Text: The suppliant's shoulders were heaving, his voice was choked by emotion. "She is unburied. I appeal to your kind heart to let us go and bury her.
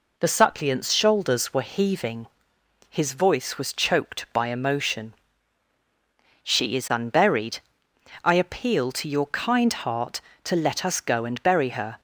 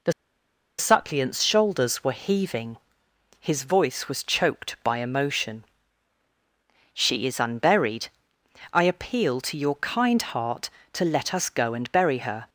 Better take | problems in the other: first | pauses between "The" and "suppliant's"; noticeable; at 0.1 s; 0.66 s long

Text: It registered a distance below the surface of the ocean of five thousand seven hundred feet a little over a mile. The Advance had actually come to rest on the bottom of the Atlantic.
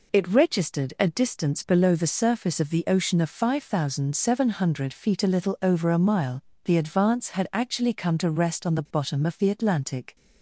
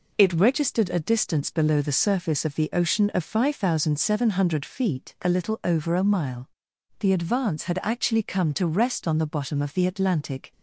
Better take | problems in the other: neither | none

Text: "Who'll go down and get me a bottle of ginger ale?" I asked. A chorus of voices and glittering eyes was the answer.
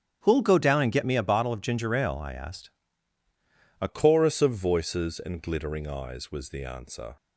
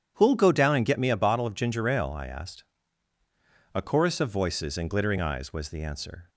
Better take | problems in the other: second | starts louder than the rest; strong; until 1.2 s; 9 dB; strong in the second // changes voice at "chorus"; from 3.8 s on; 3.3 s long

